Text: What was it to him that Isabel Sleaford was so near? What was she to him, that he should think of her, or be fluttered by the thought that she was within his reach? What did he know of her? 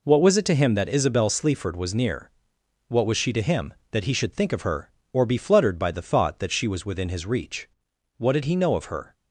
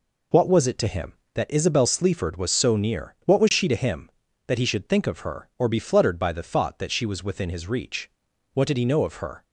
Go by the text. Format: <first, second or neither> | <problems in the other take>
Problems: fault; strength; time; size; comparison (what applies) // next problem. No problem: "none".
second | skips "so"; at 1.9 s